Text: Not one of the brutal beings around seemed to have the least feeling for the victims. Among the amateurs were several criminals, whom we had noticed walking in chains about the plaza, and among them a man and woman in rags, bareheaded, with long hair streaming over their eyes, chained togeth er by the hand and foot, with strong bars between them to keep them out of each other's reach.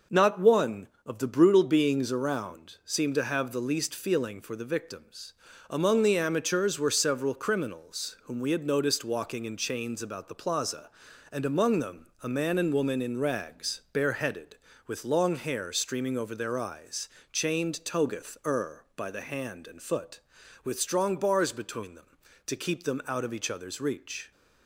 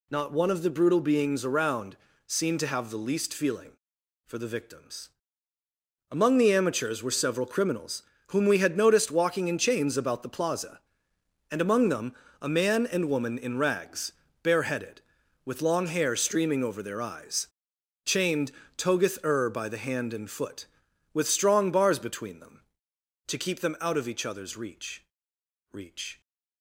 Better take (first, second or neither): first